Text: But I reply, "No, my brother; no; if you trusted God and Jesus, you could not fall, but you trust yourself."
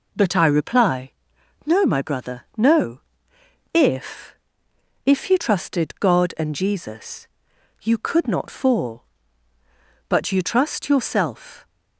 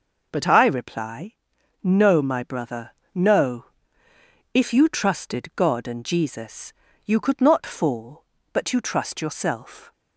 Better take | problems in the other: second | says "if" twice; at 5.0 s

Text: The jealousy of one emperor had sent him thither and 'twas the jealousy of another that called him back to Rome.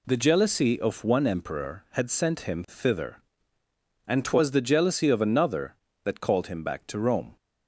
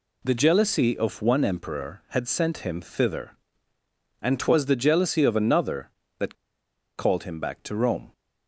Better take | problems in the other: first | pauses between "that" and "called"; noticeable; at 6.3 s; 0.62 s long

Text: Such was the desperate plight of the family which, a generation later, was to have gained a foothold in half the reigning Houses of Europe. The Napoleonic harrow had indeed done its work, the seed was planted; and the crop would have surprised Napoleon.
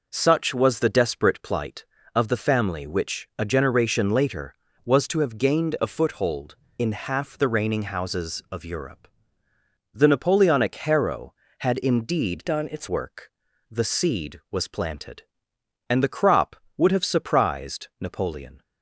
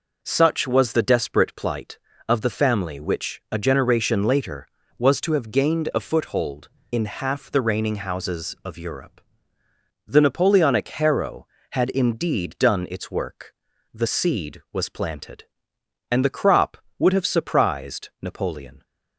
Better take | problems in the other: second | changes voice from "done" to "its"; from 12.4 to 12.8 s; 0.4 s long

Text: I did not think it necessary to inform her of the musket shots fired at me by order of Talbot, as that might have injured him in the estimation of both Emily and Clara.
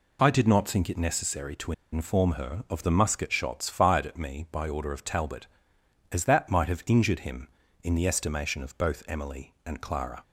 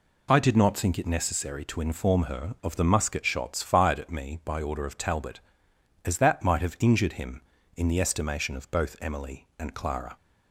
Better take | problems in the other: second | pauses between "to" and "inform"; slight; at 1.7 s; 0.20 s long

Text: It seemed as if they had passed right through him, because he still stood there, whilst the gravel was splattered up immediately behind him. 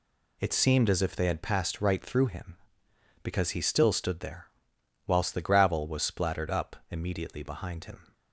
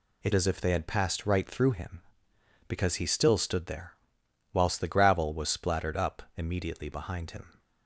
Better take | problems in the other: first | skips "seemed"; at 0.3 s

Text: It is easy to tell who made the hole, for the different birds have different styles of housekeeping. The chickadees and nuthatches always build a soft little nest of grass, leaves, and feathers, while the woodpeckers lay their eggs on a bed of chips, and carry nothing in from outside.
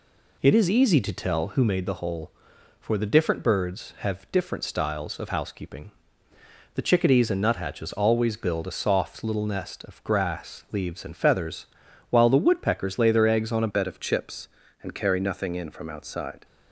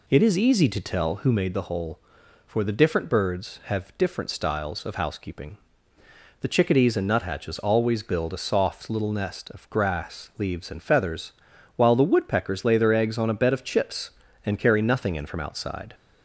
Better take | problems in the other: second | changes voice at "bed"; from 13.6 s on; 2.8 s long

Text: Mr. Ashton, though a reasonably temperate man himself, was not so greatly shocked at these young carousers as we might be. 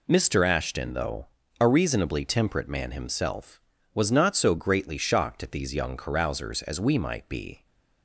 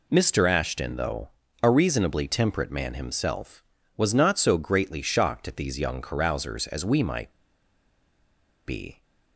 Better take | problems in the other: first | pauses between "though" and "a"; slight; at 1.3 s; 0.32 s long; slight in the first // pauses between "might" and "be"; strong; at 7.3 s; 1.3 s long

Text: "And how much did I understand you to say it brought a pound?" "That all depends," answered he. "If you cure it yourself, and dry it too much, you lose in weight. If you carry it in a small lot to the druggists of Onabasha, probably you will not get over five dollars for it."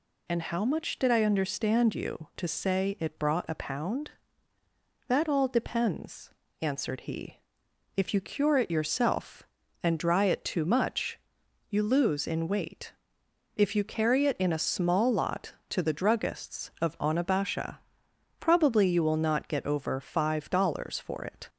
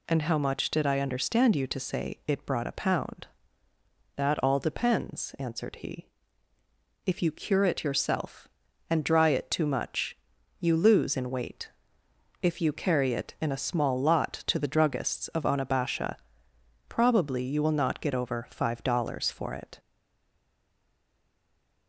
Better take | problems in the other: first | stays silent after the last word; noticeable; from 19.7 s on; 2.1 s long

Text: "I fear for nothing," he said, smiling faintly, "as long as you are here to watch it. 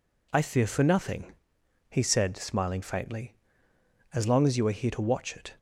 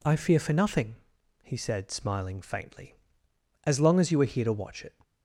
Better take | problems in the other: neither | none

